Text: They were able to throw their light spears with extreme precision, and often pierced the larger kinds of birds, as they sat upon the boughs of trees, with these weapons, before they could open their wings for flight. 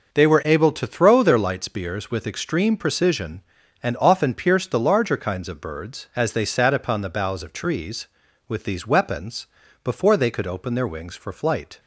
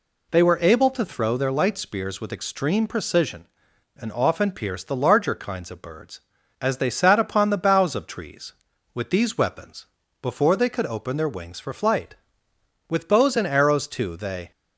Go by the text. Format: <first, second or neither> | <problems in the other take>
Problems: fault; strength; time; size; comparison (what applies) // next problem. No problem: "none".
first | goes on to say "With bows and arrows too they"; from 12.8 s on; 1.6 s long